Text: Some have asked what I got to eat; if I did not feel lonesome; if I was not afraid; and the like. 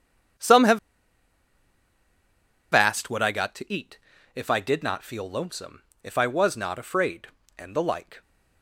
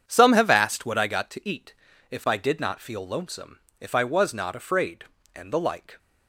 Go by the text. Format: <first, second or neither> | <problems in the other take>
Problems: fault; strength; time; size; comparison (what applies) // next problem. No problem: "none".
second | starts louder than the rest; strong; until 3.3 s; 8 dB; strong in the second // pauses between "have" and "asked"; strong; at 0.7 s; 1.9 s long